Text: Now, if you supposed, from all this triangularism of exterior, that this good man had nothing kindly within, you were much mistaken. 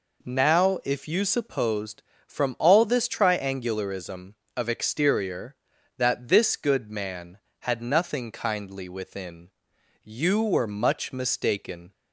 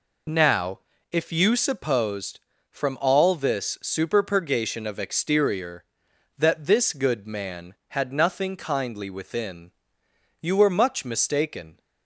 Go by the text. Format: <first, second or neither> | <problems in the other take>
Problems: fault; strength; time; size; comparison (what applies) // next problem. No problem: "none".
first | says "superpurgation" for "triangularism"; at 3.8 s